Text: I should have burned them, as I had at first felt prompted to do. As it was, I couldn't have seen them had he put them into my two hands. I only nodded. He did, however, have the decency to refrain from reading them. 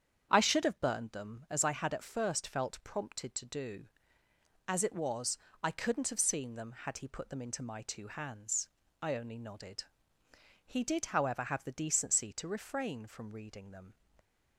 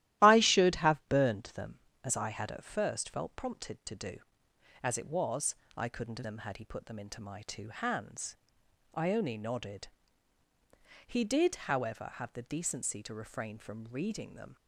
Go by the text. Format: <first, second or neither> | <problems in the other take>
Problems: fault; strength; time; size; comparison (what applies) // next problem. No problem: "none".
first | starts louder than the rest; strong; until 1.2 s; 14 dB; strong in the first // skips "seen"; at 6.2 s